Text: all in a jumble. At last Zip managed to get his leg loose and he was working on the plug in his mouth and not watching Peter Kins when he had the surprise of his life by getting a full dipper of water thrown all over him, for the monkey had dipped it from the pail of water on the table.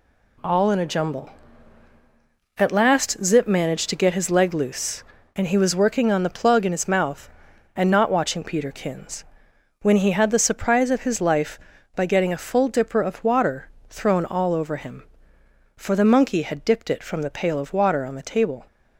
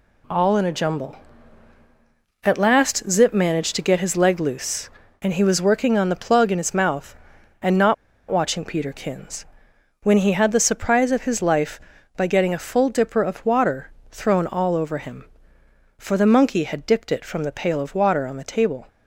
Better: first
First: pauses between "Kins" and "when"; noticeable; at 9.2 s; 0.58 s long // pauses between "water" and "thrown"; slight; at 13.6 s; 0.20 s long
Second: pauses between "not" and "watching"; slight; at 7.9 s; 0.35 s long // pauses between "Kins" and "when"; noticeable; at 9.4 s; 0.58 s long // pauses between "water" and "thrown"; slight; at 13.9 s; 0.20 s long

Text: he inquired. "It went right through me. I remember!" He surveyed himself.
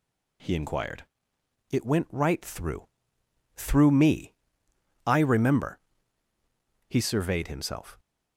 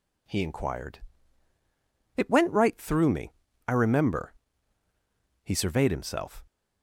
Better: second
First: says "through" twice; at 3.5 s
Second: none

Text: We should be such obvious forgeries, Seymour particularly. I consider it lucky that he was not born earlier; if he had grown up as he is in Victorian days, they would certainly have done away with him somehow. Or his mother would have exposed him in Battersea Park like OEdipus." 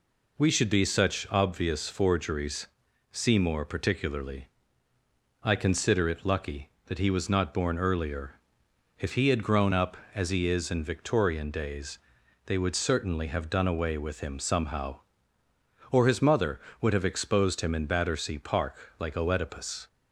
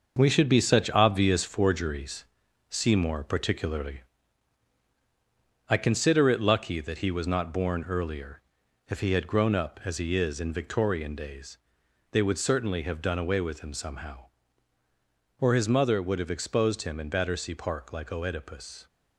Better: first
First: none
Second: gets quieter; strong; throughout; 7.5 dB

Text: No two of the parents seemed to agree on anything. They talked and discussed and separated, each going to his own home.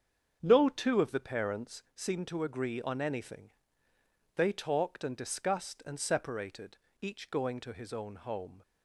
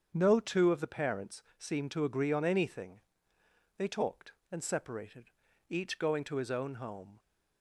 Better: first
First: starts louder than the rest; strong; until 1.4 s; 7.5 dB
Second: starts louder than the rest; strong; until 1.1 s; 7.5 dB // pauses between "parents" and "seemed"; slight; at 1.4 s; 0.16 s long // skips "and discussed"; at 4.4 s

